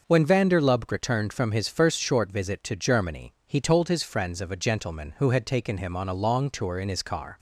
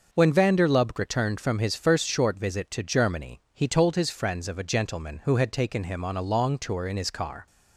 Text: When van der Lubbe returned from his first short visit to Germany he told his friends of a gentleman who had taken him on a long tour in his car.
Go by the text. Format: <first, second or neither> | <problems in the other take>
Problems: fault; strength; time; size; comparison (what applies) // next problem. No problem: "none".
neither | starts louder than the rest; noticeable; the same in both